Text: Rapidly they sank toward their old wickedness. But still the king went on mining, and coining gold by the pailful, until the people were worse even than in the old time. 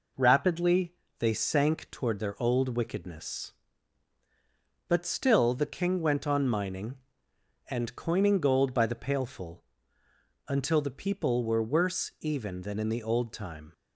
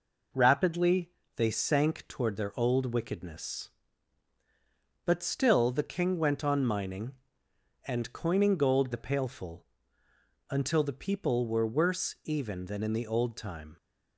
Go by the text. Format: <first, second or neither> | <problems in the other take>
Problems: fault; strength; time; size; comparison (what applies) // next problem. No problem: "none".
first | pauses between "Rapidly" and "they"; slight; at 1.0 s; 0.28 s long; slight in the first // skips "by"; at 8.9 s